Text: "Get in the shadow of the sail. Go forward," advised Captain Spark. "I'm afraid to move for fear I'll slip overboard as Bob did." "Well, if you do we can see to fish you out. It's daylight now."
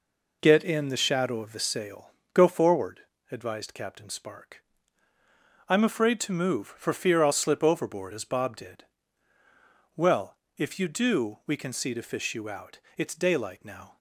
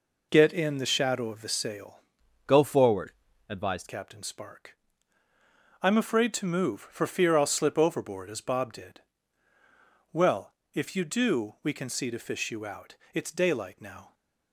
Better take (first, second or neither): first